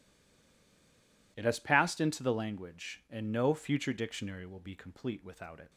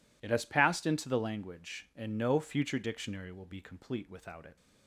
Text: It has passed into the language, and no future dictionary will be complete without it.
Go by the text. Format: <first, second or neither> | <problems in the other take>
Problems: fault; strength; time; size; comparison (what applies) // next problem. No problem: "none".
second | stays silent before the first word; noticeable; until 1.3 s; 1.3 s long